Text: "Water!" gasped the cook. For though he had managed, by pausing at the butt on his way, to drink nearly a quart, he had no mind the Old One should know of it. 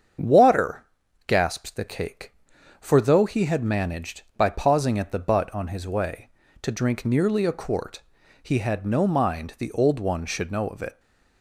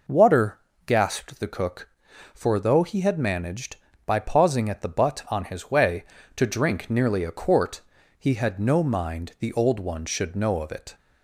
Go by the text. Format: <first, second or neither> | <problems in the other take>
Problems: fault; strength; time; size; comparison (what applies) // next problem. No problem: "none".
second | starts louder than the rest; strong; until 1.6 s; 7.5 dB // says "cake" for "cook"; at 1.8 s